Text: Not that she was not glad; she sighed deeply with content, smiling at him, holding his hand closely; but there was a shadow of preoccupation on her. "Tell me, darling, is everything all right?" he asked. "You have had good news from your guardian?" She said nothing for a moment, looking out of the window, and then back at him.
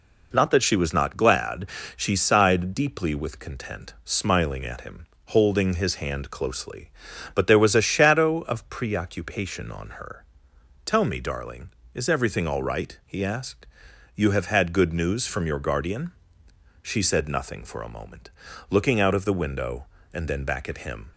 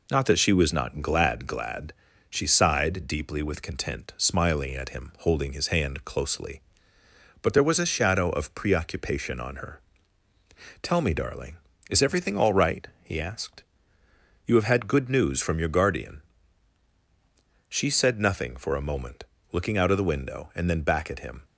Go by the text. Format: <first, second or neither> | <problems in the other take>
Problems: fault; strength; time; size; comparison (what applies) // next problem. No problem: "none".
first | says "glad" twice; at 1.4 s